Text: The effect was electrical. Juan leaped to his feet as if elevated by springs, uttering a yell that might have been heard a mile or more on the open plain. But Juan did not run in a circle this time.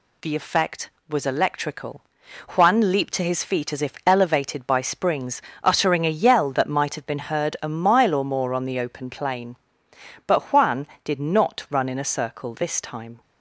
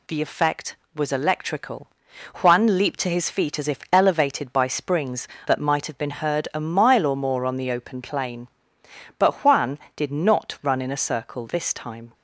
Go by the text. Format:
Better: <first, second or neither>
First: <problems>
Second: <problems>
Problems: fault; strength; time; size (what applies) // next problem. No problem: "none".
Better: first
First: none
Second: skips "uttering a yell"; at 5.3 s